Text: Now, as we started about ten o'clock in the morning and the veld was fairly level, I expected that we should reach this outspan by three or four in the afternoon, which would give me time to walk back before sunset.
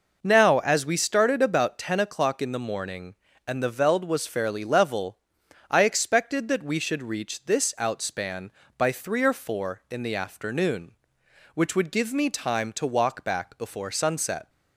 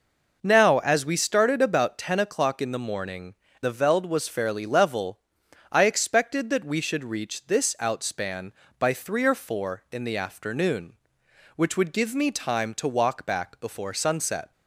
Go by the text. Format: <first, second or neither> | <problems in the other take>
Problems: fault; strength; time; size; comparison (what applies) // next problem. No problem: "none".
first | skips "and"; at 3.4 s